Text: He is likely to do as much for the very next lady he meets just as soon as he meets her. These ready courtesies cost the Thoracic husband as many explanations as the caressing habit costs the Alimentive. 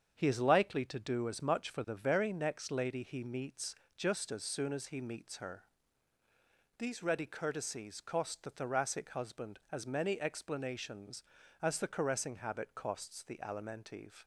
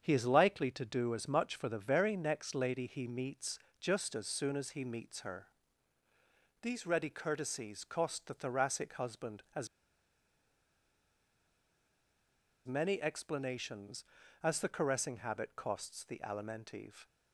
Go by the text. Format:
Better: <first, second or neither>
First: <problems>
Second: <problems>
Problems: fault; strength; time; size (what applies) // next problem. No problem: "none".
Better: first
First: starts louder than the rest; strong; until 1.1 s; 7.5 dB // pauses between "meets" and "just"; slight; at 3.7 s; 0.20 s long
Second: starts louder than the rest; strong; until 1.0 s; 7.5 dB // pauses between "meets" and "just"; slight; at 3.5 s; 0.20 s long // pauses between "as" and "many"; strong; at 9.6 s; 2.9 s long